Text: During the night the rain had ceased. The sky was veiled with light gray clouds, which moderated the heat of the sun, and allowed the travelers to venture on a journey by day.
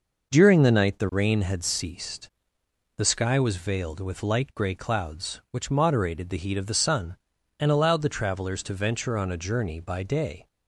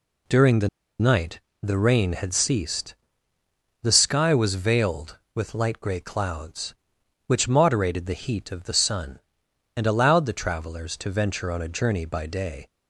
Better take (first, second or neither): first